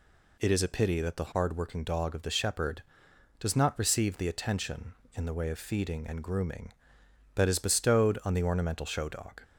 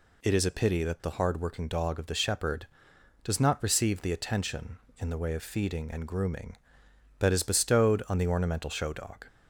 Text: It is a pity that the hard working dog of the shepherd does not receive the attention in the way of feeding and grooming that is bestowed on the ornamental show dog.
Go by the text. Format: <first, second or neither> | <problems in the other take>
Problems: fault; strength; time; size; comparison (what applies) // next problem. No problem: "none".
neither | none